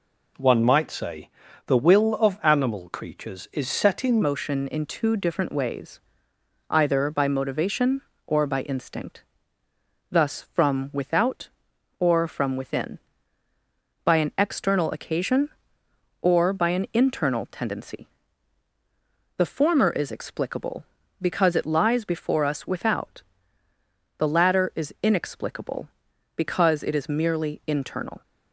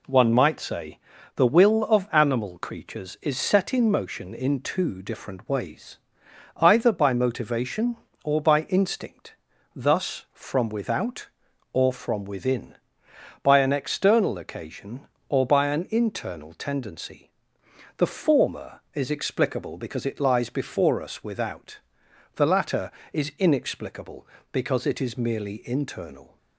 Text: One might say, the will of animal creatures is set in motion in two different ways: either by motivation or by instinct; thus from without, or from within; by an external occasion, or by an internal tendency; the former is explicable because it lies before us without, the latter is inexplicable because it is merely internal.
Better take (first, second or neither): second